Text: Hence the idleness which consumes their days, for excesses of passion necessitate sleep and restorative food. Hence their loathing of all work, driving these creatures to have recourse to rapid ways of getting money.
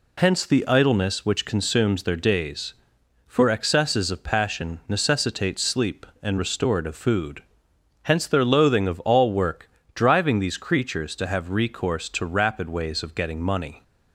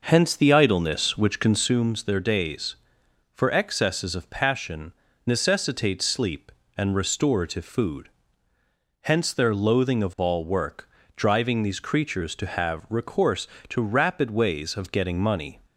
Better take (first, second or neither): first